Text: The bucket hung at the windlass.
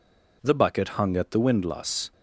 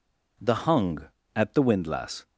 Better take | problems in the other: first | skips "bucket"; at 0.5 s

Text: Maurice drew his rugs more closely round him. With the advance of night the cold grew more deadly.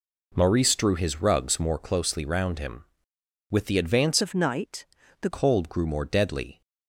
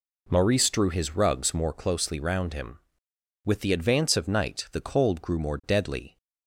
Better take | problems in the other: second | changes voice from "of" to "the"; from 4.2 to 5.2 s; 1.0 s long // pauses between "night" and "the"; slight; at 4.8 s; 0.34 s long

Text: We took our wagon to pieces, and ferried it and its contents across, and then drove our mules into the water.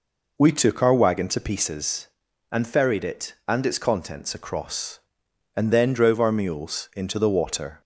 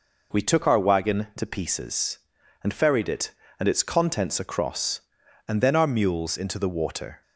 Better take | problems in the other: first | skips "drove"; at 5.7 s

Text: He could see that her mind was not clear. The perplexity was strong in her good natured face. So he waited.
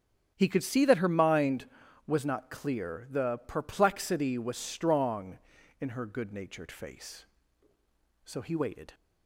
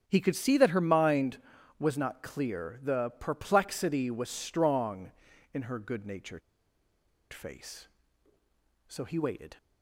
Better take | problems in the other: first | starts louder than the rest; strong; until 1.0 s; 9 dB; strong in the first // pauses between "natured" and "face"; noticeable; at 6.4 s; 0.92 s long

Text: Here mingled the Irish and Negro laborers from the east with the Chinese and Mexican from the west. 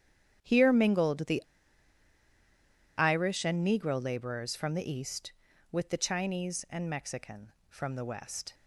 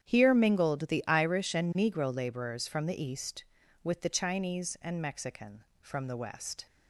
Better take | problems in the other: second | starts louder than the rest; strong; until 1.4 s; 9 dB; strong in the second // pauses between "the" and "Irish"; strong; at 1.4 s; 1.5 s long

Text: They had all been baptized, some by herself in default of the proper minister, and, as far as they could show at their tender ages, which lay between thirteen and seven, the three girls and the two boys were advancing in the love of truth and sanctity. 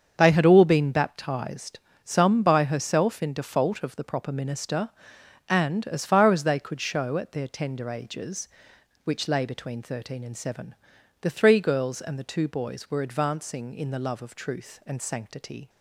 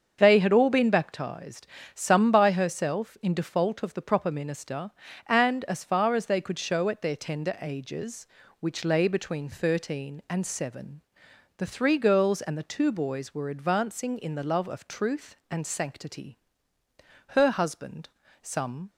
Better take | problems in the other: first | starts louder than the rest; until 1.2 s; 7 dB; strong in the first // goes on to say "Her husband some"; from 17.2 s on; 1.6 s long

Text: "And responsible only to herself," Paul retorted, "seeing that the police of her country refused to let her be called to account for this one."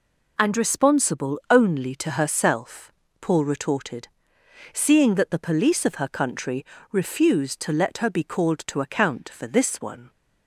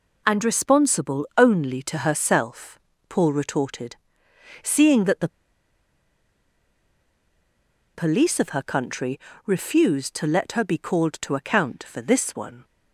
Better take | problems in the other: first | pauses between "the" and "police"; strong; at 5.2 s; 2.6 s long // pauses between "country" and "refused"; slight; at 9.2 s; 0.24 s long; slight in the first

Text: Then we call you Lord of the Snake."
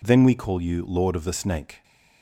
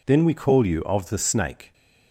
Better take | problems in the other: first | skips "Lord"; at 0.8 s

